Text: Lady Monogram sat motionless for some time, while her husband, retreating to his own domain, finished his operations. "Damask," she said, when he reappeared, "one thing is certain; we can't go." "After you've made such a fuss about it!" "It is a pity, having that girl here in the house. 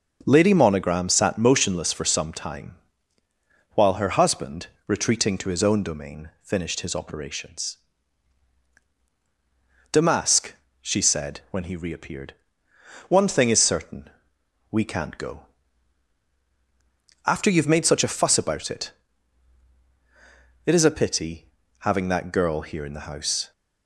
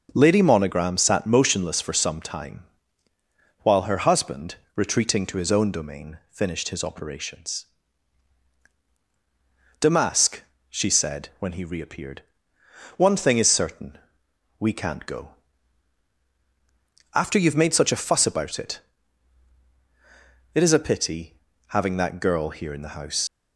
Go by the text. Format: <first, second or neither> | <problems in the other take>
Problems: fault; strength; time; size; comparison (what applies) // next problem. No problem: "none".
first | starts louder than the rest; until 1.1 s; 6.5 dB; also in the first // leaves "house" unfinished; at 23.2 s; 130 ms